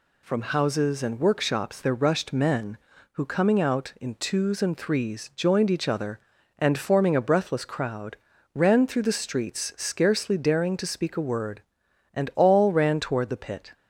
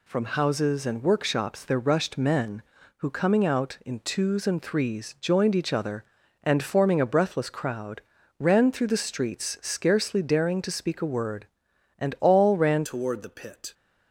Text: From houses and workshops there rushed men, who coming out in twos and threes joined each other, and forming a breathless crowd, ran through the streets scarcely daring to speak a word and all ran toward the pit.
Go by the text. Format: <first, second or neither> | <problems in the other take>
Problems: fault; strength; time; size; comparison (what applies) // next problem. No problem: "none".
first | changes voice at "toward"; from 12.8 s on; 0.9 s long